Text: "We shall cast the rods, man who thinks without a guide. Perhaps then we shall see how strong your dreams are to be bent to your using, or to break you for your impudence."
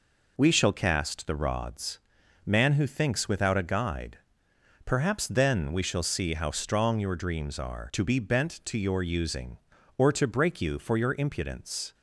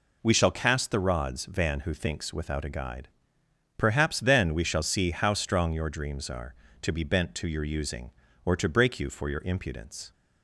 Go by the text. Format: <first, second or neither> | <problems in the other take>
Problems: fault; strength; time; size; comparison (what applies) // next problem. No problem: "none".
first | says "van" for "man"; at 1.4 s